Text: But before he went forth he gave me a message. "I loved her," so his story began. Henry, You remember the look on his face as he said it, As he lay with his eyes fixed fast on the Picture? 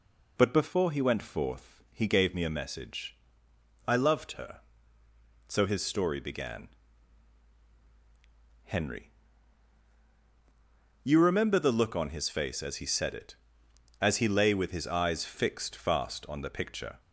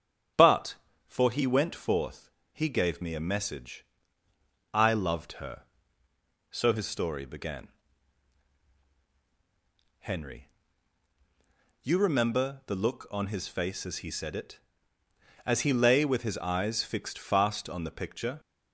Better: first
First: none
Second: starts louder than the rest; strong; until 1.6 s; 8 dB // says "for" for "before"; at 1.0 s // pauses between "forth" and "he"; slight; at 2.2 s; 0.22 s long

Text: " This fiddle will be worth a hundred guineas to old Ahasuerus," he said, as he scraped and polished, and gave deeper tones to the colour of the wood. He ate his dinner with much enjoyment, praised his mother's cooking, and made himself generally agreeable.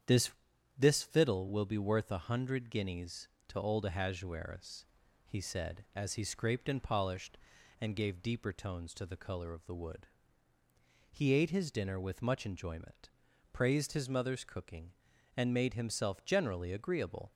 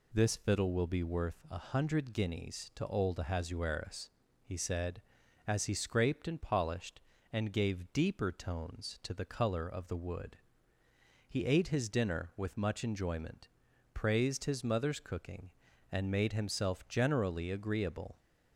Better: second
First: starts louder than the rest; strong; until 1.4 s; 8.5 dB // says "This" twice; at 0.7 s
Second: none

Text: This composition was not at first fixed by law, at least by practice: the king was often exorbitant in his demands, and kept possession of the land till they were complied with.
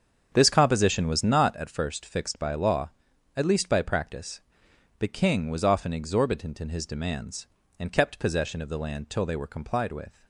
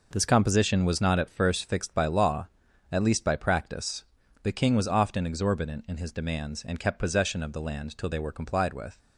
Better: second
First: starts louder than the rest; strong; until 1.6 s; 7.5 dB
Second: none

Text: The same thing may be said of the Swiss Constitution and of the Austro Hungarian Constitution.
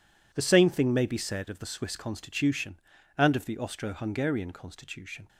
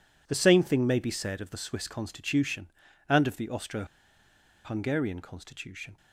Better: first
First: none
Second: pauses between "Austro" and "Hungarian"; noticeable; at 3.8 s; 0.79 s long

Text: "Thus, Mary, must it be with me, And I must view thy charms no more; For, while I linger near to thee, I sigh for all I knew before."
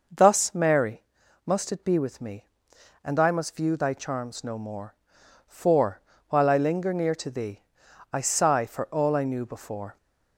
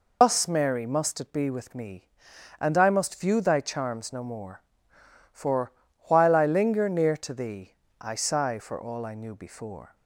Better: first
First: none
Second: loses the start of "Thus"; at 0.2 s; 145 ms

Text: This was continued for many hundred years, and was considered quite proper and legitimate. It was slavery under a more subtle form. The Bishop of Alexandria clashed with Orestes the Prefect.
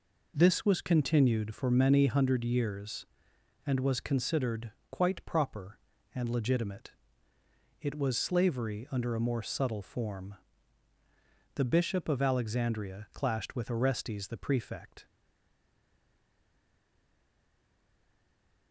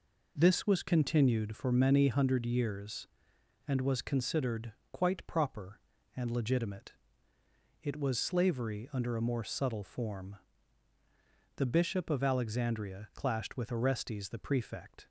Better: second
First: pauses between "considered" and "quite"; slight; at 4.7 s; 0.20 s long // stays silent after the last word; strong; from 15.0 s on; 3.7 s long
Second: pauses between "considered" and "quite"; slight; at 4.7 s; 0.20 s long

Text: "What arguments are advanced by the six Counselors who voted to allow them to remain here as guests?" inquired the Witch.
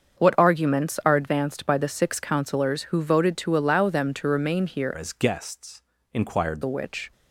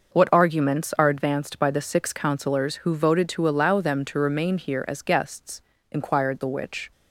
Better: second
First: starts louder than the rest; until 1.2 s; 7 dB // changes voice from "as" to "inquired"; from 4.9 to 6.6 s; 1.7 s long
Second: none

